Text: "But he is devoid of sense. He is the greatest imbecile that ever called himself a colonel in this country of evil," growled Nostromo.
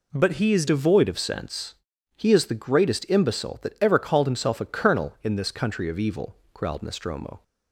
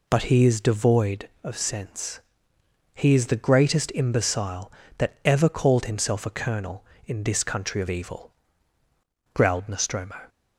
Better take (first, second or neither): second